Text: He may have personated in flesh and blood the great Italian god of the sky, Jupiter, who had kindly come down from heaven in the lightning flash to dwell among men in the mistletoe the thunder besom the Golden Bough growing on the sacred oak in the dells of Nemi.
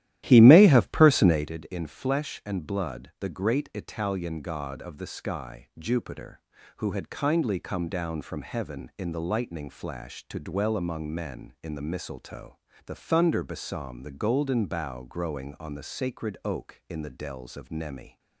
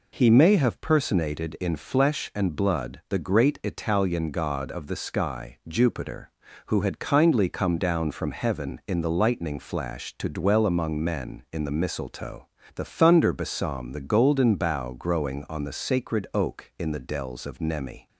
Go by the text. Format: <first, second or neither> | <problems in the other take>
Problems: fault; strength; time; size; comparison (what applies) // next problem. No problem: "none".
second | starts louder than the rest; strong; until 1.5 s; 13.5 dB // pauses between "mistletoe" and "the"; slight; at 12.5 s; 0.30 s long; slight in the second